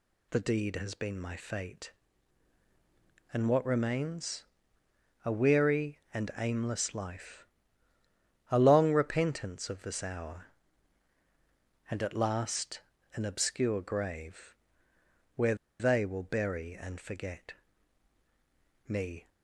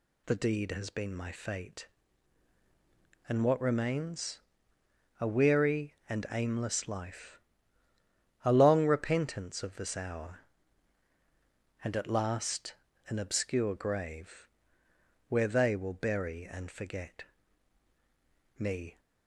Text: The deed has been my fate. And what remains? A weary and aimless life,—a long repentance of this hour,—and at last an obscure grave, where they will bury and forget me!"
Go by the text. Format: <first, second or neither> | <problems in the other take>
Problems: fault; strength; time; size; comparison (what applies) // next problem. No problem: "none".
second | pauses between "last" and "an"; slight; at 12.8 s; 0.34 s long; slight in the second // pauses between "where" and "they"; slight; at 15.5 s; 0.25 s long // pauses between "forget" and "me"; strong; at 17.5 s; 1.3 s long; strong in the second